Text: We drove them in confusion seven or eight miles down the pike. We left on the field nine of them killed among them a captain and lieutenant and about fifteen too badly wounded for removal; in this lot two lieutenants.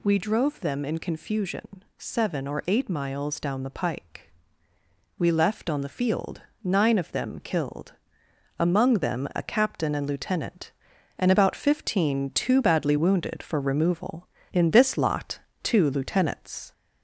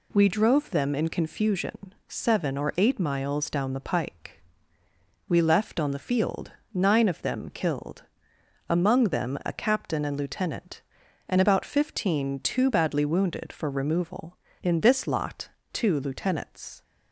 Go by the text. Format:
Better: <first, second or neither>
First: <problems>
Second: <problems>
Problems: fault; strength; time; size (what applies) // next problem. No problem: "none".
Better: second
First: gets louder; slight; throughout; 3 dB // pauses between "confusion" and "seven"; slight; at 1.8 s; 0.16 s long // pauses between "field" and "nine"; slight; at 6.4 s; 0.22 s long // pauses between "killed" and "among"; noticeable; at 7.9 s; 0.66 s long // pauses between "lot" and "two"; slight; at 15.3 s; 0.24 s long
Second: pauses between "confusion" and "seven"; slight; at 1.9 s; 0.16 s long // pauses between "field" and "nine"; slight; at 6.5 s; 0.22 s long // pauses between "killed" and "among"; noticeable; at 8.0 s; 0.66 s long // pauses between "lot" and "two"; slight; at 15.4 s; 0.24 s long